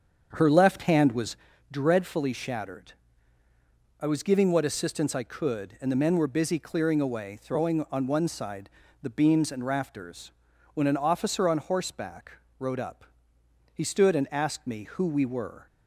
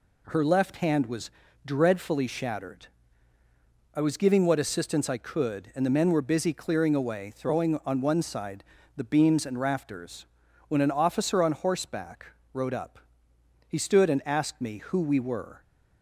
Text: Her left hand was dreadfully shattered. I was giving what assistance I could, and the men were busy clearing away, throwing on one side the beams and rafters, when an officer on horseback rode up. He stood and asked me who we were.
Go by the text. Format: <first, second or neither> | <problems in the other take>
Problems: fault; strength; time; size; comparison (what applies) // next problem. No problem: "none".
second | starts louder than the rest; strong; until 1.5 s; 7.5 dB // pauses between "was" and "dreadfully"; slight; at 1.3 s; 0.36 s long; slight in the second // pauses between "side" and "the"; slight; at 8.7 s; 0.32 s long; slight in the second // pauses between "horseback" and "rode"; slight; at 12.3 s; 0.26 s long; slight in the second